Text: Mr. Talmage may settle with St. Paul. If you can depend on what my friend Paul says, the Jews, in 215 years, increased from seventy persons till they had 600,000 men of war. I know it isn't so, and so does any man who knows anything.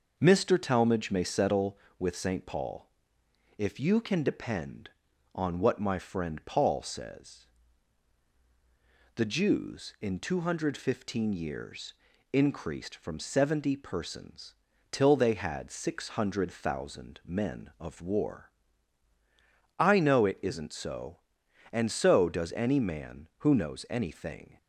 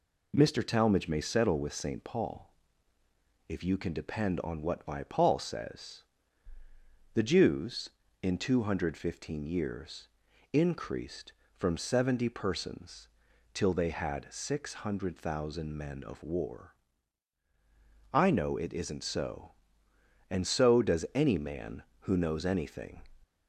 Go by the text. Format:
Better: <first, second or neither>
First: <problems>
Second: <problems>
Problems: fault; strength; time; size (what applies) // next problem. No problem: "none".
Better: first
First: pauses between "persons" and "till"; slight; at 14.5 s; 0.34 s long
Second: skips "friend"; at 5.0 s // pauses between "persons" and "till"; noticeable; at 13.0 s; 0.46 s long